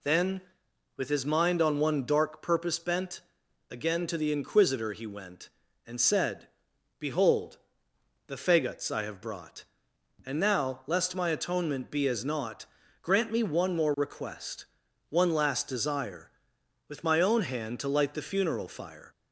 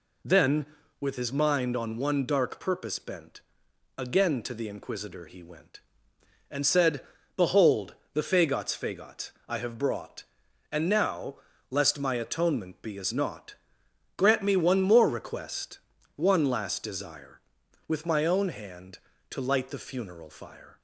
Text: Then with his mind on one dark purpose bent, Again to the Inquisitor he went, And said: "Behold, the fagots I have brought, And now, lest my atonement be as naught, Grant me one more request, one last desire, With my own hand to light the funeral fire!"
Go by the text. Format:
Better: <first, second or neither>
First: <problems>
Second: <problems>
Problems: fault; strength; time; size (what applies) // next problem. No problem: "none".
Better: first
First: none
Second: says "fagots" twice; at 8.7 s